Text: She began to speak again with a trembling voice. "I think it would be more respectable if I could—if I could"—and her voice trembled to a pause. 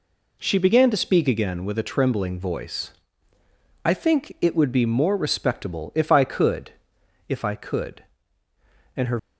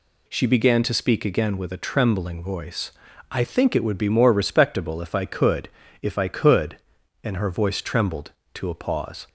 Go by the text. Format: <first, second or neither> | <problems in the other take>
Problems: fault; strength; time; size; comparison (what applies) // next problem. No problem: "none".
second | stops before "voice trembled to a pause"; at 9.1 s